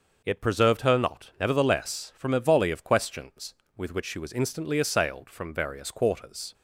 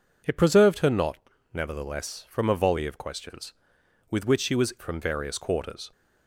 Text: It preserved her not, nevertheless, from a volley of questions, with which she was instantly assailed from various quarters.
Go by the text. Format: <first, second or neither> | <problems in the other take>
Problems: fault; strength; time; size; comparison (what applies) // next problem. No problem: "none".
first | skips "instantly assailed"; at 4.7 s